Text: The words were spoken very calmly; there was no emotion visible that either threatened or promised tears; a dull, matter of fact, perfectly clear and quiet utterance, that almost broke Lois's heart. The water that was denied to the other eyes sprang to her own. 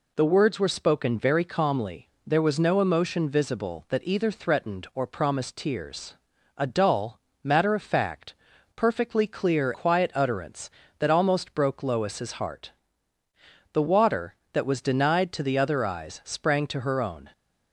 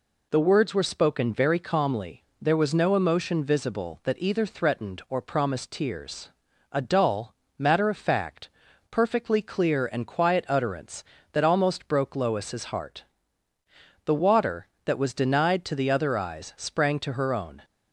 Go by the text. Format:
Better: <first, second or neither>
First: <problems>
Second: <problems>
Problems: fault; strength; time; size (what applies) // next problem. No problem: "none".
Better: second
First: skips "and"; at 9.7 s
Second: none